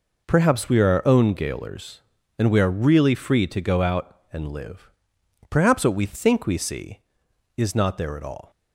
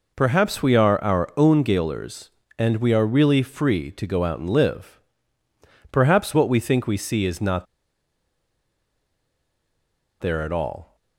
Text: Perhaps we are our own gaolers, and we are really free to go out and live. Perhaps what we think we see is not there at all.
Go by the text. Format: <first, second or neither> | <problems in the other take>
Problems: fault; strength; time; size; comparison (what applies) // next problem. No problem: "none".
first | pauses between "not" and "there"; strong; at 7.6 s; 2.5 s long